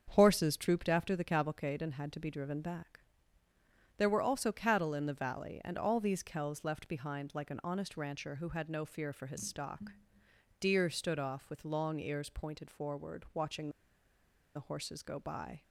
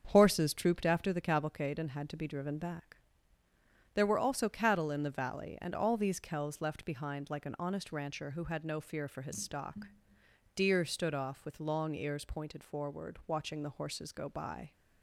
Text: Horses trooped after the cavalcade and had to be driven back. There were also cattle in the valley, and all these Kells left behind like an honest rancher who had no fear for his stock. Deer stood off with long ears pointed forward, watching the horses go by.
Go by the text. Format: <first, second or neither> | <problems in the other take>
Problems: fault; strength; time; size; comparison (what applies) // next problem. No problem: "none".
second | starts louder than the rest; strong; until 1.1 s; 7 dB; strong in the second // pauses between "watching" and "the"; noticeable; at 13.6 s; 0.86 s long